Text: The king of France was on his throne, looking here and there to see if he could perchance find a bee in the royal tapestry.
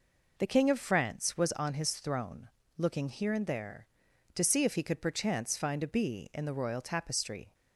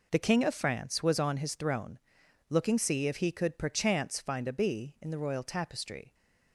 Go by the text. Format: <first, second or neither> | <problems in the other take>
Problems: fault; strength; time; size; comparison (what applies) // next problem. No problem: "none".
first | skips "here and there to"; at 2.7 s